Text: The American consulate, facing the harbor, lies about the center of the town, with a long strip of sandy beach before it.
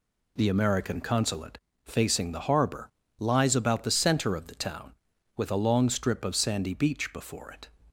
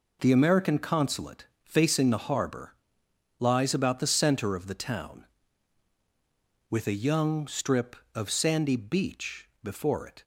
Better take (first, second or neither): first